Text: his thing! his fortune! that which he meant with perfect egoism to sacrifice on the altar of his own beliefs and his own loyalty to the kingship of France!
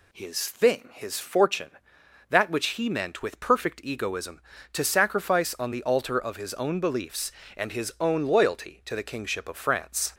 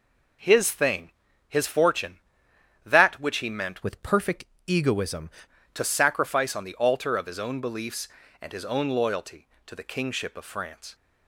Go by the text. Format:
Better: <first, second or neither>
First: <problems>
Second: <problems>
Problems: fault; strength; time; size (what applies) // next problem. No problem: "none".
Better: first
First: none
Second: changes voice from "with" to "egoism"; from 3.8 to 5.2 s; 1.4 s long // pauses between "perfect" and "egoism"; slight; at 4.4 s; 0.24 s long